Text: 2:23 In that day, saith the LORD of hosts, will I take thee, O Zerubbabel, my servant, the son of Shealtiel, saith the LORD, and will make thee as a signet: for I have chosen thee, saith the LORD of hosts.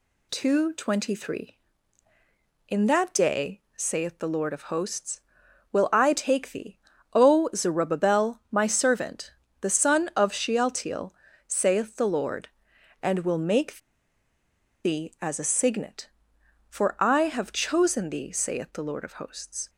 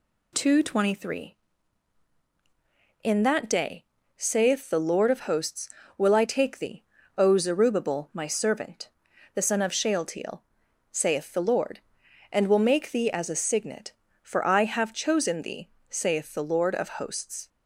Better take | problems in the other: second | pauses between "make" and "thee"; at 13.7 s; 1.0 s long

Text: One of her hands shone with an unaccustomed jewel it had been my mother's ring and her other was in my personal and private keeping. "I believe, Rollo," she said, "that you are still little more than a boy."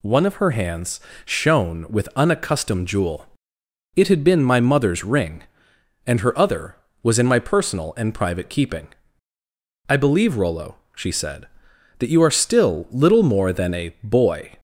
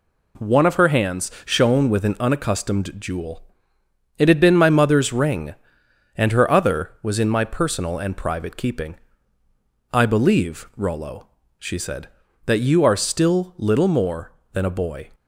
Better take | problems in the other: second | pauses between "hands" and "shone"; slight; at 0.9 s; 0.26 s long // skips "an"; at 2.1 s // pauses between "jewel" and "it"; noticeable; at 3.2 s; 0.70 s long; noticeable in the second

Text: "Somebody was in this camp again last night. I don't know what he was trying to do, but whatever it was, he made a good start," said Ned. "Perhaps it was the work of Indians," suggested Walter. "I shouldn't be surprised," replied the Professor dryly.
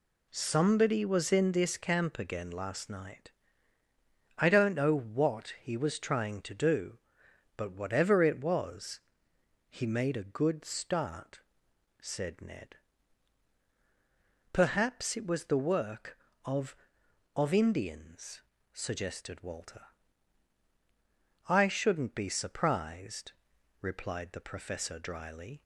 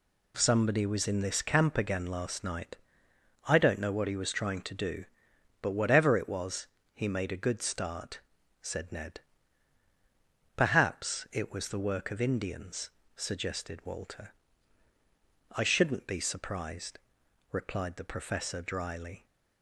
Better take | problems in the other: second | says "of" twice; at 17.3 s

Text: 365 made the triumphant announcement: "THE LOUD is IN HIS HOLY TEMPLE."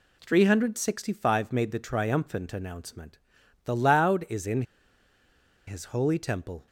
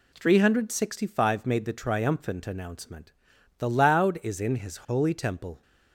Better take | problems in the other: second | pauses between "IN" and "HIS"; at 4.6 s; 1.0 s long

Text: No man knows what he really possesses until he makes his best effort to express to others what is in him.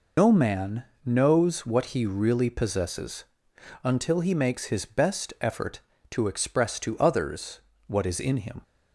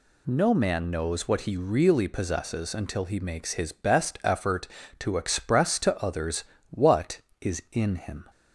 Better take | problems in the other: second | loses the start of "No"; at 0.1 s; 85 ms // pauses between "man" and "knows"; slight; at 0.8 s; 0.20 s long // pauses between "possesses" and "until"; noticeable; at 3.2 s; 0.58 s long // pauses between "others" and "what"; slight; at 7.5 s; 0.28 s long; slight in the second

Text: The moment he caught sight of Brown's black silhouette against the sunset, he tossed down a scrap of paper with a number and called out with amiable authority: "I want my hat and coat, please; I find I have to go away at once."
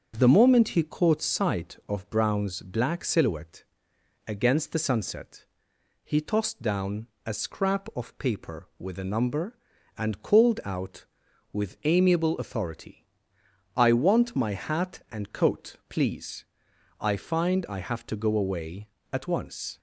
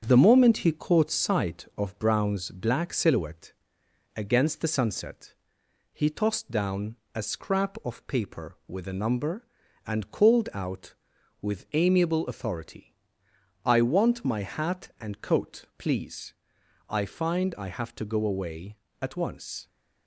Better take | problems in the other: first | gets quieter; throughout; 4 dB // starts louder than the rest; strong; until 1.0 s; 7.5 dB; also in the first // pauses between "silhouette" and "against"; noticeable; at 3.5 s; 0.64 s long; noticeable in the first // pauses between "down" and "a"; slight; at 6.9 s; 0.20 s long; slight in the first

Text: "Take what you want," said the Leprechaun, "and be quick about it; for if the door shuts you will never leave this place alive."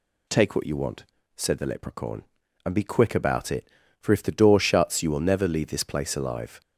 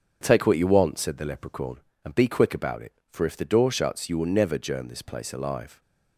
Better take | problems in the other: first | starts louder than the rest; until 1.2 s; 7 dB // says "germ" for "leave"; at 4.5 s

